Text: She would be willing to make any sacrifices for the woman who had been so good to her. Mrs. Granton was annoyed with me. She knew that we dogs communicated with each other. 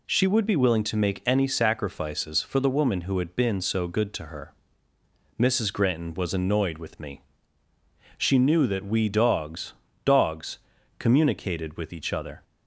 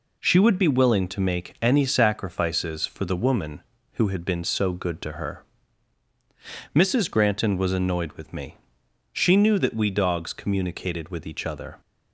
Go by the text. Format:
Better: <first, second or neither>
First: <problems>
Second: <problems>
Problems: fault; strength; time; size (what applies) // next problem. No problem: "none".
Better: second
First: says "dogs" twice; at 10.0 s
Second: none